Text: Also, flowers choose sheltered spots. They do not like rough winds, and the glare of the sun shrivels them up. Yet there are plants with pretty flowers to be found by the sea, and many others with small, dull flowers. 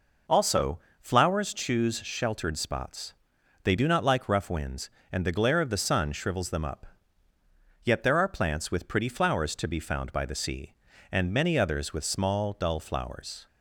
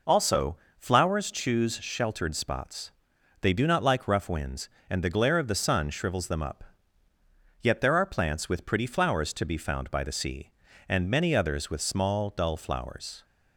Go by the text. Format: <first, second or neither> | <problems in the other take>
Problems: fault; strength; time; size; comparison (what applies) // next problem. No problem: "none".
neither | none